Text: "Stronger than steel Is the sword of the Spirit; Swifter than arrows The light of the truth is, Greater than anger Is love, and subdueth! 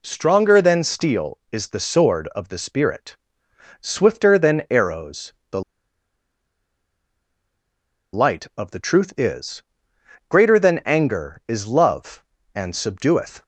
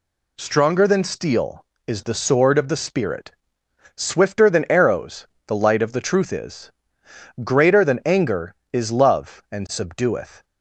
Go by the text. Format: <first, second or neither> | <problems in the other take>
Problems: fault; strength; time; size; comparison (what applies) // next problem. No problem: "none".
second | pauses between "arrows" and "The"; slight; at 5.3 s; 0.18 s long; slight in the second // pauses between "The" and "light"; strong; at 5.6 s; 2.5 s long